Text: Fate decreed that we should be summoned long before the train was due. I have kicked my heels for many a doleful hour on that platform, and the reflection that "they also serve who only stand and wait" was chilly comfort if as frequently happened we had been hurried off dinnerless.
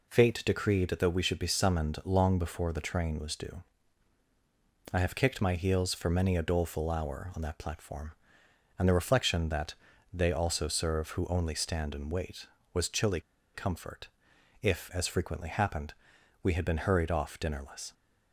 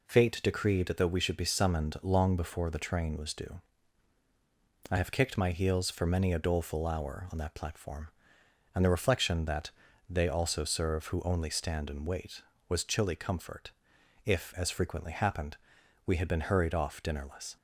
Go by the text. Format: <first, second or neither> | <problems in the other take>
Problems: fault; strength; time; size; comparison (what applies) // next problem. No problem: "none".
second | pauses between "that" and "they"; slight; at 9.7 s; 0.36 s long; slight in the second // pauses between "chilly" and "comfort"; slight; at 13.2 s; 0.33 s long // pauses between "comfort" and "if"; noticeable; at 14.0 s; 0.56 s long; noticeable in the second // pauses between "happened" and "we"; noticeable; at 15.9 s; 0.48 s long; noticeable in the second